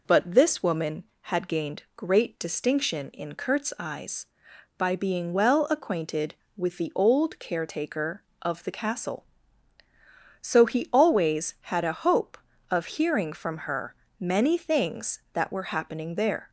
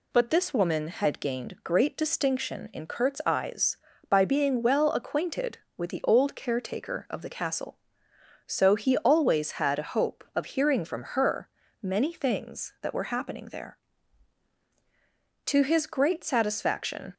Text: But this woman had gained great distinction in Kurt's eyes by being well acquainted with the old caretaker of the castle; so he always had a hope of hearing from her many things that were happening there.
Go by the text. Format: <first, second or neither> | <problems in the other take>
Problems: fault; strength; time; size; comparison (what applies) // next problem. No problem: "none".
first | pauses between "her" and "many"; slight; at 11.4 s; 0.34 s long; slight in the first // goes on to say "To his great satisfaction"; strong; from 15.4 s on; 1.6 s long